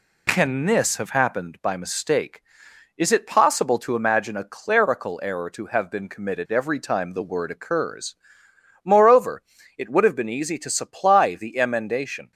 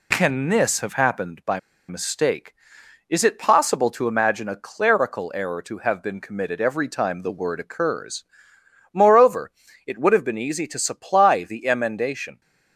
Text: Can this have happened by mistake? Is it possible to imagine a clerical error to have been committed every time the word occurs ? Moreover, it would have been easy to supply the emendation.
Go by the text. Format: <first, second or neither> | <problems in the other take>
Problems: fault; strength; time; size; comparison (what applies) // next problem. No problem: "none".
first | pauses between "by" and "mistake"; slight; at 1.5 s; 0.28 s long